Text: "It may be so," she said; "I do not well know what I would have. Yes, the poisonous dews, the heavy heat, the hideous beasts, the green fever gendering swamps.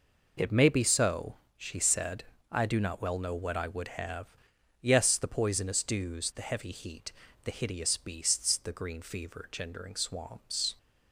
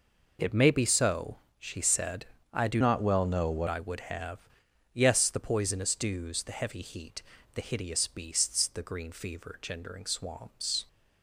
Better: first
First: none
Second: changes voice from "not" to "what"; from 2.8 to 3.6 s; 0.8 s long

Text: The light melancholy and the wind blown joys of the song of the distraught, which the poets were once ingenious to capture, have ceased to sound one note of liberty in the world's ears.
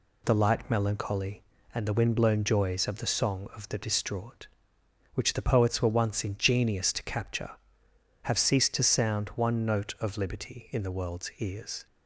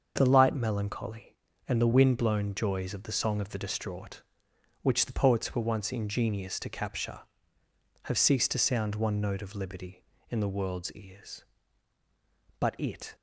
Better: first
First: none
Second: starts louder than the rest; until 1.1 s; 6.5 dB // goes on to say "But it"; from 12.6 s on; 0.54 s long

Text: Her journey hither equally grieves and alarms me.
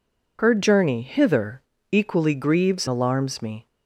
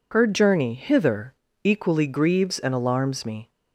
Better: second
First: pauses between "hither" and "equally"; slight; at 1.5 s; 0.32 s long // skips "and"; at 2.8 s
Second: pauses between "hither" and "equally"; slight; at 1.3 s; 0.32 s long

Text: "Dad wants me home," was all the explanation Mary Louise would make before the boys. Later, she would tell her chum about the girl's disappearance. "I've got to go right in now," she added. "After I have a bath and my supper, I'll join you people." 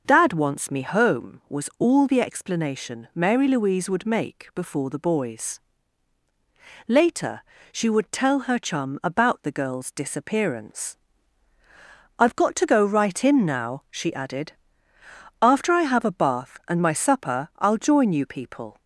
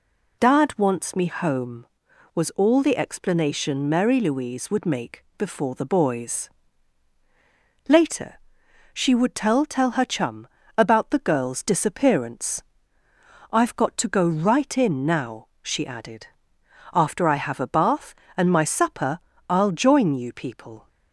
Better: first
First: none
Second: says "tell" twice; at 9.6 s // pauses between "chum" and "about"; slight; at 10.4 s; 0.30 s long

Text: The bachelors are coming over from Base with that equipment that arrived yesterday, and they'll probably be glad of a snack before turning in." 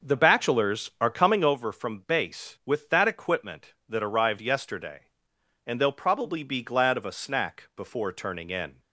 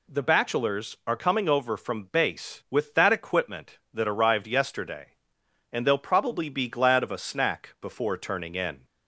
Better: second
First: starts louder than the rest; noticeable; until 1.6 s; 6 dB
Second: none

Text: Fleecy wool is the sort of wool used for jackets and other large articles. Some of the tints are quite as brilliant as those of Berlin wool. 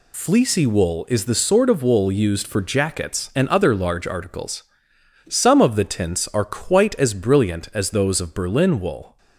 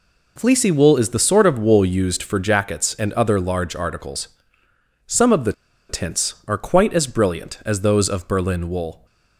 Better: first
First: none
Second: pauses between "the" and "tints"; at 5.5 s; 0.36 s long

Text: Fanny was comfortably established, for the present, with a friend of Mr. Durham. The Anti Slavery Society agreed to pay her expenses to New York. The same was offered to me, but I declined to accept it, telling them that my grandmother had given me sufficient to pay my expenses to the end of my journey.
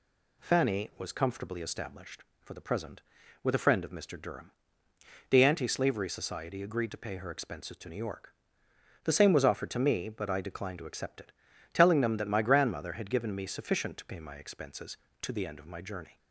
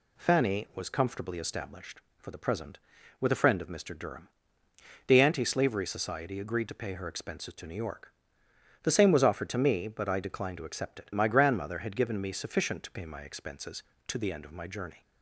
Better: first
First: none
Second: skips "telling them that"; at 11.1 s

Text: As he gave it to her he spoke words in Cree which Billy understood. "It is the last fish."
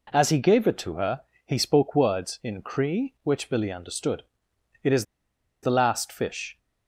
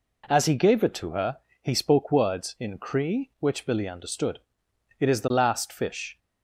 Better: second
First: pauses between "her" and "he"; slight; at 1.2 s; 0.24 s long // pauses between "is" and "the"; noticeable; at 5.0 s; 0.58 s long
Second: pauses between "her" and "he"; slight; at 1.3 s; 0.24 s long

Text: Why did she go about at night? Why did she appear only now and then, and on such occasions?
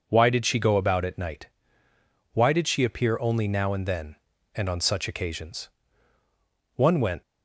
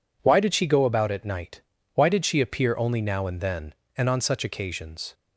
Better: second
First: goes on to say "One went"; slight; from 6.7 s on; 0.46 s long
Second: none

